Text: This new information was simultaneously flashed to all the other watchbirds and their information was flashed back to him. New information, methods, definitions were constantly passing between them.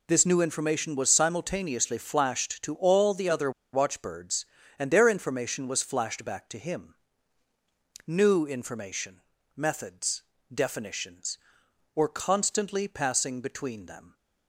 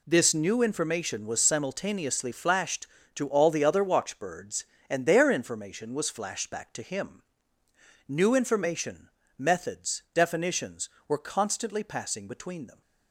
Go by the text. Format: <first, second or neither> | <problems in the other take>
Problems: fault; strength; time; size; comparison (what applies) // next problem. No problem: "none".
second | pauses between "other" and "watchbirds"; slight; at 3.5 s; 0.21 s long